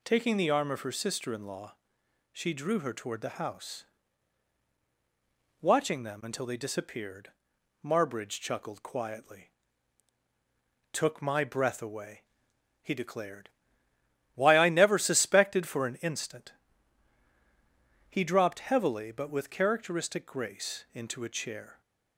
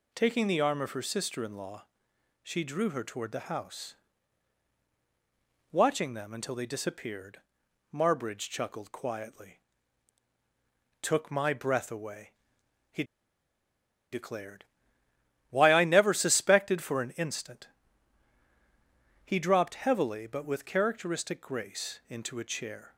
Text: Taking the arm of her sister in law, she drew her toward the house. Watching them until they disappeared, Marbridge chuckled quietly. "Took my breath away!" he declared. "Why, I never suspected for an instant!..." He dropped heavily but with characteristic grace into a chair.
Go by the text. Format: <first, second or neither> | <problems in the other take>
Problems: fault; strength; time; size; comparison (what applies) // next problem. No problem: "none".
first | pauses between "he" and "declared"; at 13.0 s; 1.0 s long